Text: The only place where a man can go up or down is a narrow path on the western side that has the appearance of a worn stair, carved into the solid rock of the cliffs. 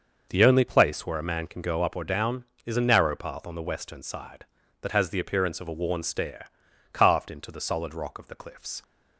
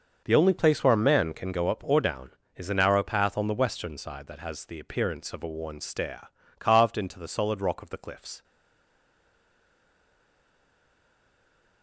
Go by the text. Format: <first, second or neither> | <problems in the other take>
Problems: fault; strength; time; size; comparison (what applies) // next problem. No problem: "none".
first | starts louder than the rest; noticeable; until 1.2 s; 6 dB; noticeable in the first // stays silent after the last word; strong; from 8.4 s on; 3.4 s long